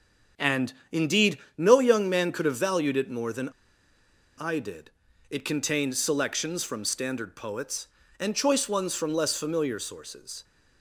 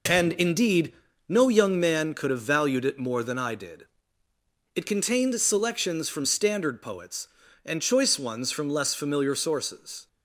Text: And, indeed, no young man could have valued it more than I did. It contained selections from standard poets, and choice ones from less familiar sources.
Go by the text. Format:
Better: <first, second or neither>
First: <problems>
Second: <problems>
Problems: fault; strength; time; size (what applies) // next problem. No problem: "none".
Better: second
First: starts louder than the rest; until 1.7 s; 6.5 dB // pauses between "than" and "I"; noticeable; at 3.4 s; 0.90 s long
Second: none